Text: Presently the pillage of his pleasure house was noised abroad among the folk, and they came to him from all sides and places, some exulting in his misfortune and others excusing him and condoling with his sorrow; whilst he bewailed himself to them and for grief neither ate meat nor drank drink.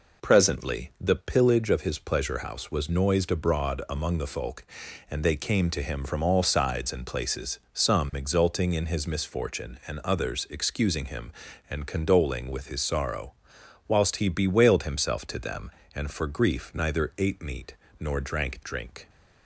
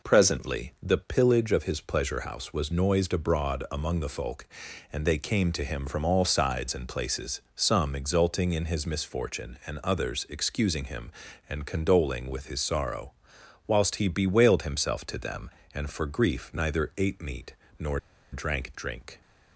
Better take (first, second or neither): first